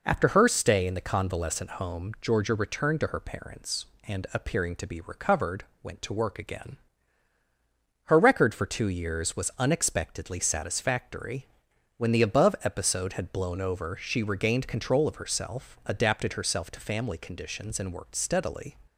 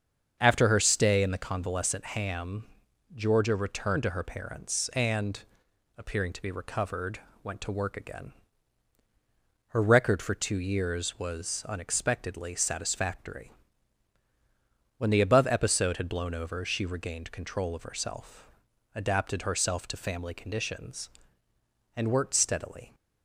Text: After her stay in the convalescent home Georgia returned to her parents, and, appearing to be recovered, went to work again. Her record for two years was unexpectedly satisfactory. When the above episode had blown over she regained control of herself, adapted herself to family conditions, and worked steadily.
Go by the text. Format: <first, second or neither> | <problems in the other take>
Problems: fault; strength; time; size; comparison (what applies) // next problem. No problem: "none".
first | starts louder than the rest; until 1.4 s; 7 dB // says "ham" for "home"; at 2.0 s